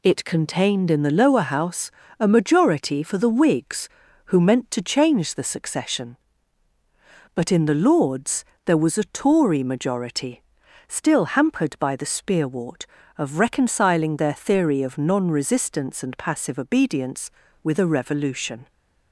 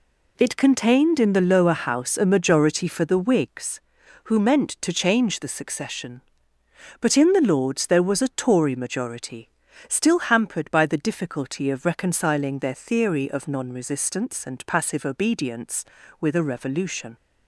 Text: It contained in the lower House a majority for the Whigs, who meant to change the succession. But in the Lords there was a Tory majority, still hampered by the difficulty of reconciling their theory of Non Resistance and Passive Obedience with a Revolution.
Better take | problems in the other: second | pauses between "House" and "a"; slight; at 1.9 s; 0.28 s long // pauses between "Lords" and "there"; slight; at 8.4 s; 0.20 s long // says "spearwort" for "difficulty"; at 12.0 s

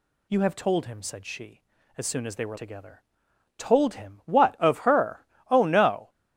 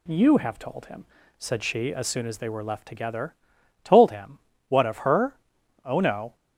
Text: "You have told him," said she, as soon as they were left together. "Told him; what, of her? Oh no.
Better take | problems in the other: second | skips "left"; at 2.5 s

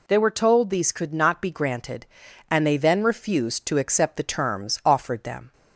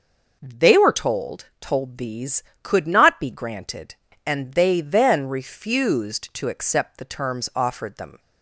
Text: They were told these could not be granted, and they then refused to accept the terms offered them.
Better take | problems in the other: first | says "told" twice; at 1.5 s

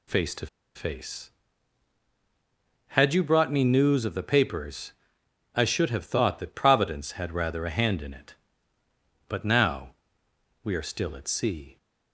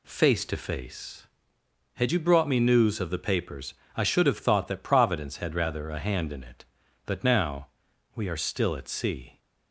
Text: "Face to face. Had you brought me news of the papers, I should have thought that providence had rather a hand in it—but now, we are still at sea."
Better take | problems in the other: second | pauses between "to" and "face"; slight; at 0.4 s; 0.28 s long

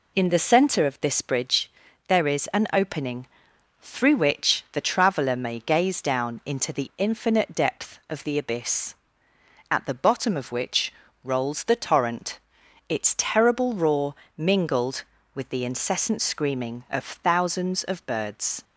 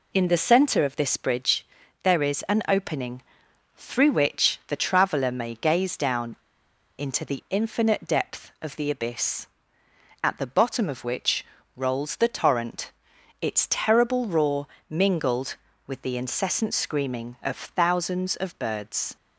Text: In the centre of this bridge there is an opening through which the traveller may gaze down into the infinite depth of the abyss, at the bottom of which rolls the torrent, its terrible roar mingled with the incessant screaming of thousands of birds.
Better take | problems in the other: first | pauses between "bridge" and "there"; at 1.6 s; 0.38 s long; also in the first // pauses between "opening" and "through"; noticeable; at 3.2 s; 0.52 s long; noticeable in the first // pauses between "down" and "into"; noticeable; at 6.3 s; 0.63 s long // pauses between "which" and "rolls"; slight; at 11.4 s; 0.32 s long; slight in the first // pauses between "roar" and "mingled"; slight; at 14.6 s; 0.20 s long; slight in the first

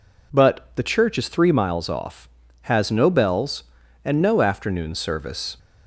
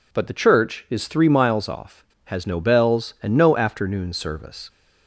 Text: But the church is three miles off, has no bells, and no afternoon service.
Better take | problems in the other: neither | none

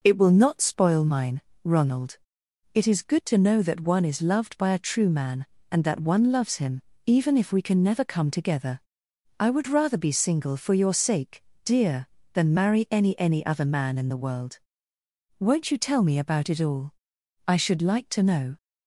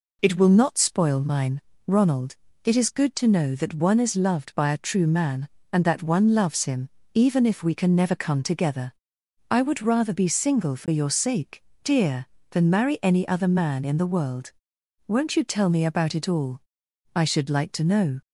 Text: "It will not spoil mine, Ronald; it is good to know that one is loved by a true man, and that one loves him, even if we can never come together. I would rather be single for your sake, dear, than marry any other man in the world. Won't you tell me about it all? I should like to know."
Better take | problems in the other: second | says "any" twice; at 13.1 s

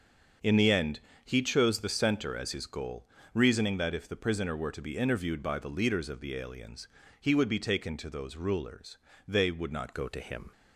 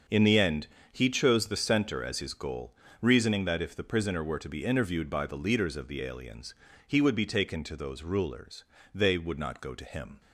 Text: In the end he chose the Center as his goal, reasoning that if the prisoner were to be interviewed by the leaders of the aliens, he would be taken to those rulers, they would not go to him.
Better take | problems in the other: second | starts louder than the rest; until 1.6 s; 6.5 dB; also in the second // pauses between "end" and "he"; slight; at 0.9 s; 0.26 s long; slight in the second // changes voice at "go"; from 9.9 s on; 0.6 s long

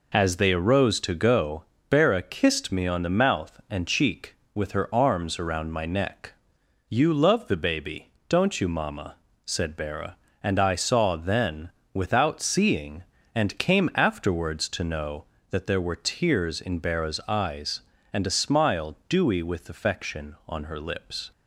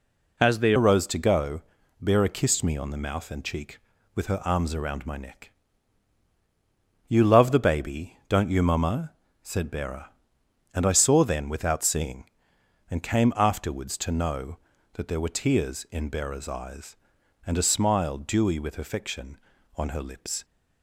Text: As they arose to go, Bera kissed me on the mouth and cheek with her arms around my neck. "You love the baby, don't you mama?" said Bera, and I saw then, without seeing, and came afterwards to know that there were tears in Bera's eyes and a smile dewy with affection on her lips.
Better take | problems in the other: first | changes voice at "arose"; from 0.7 s on; 19.7 s long

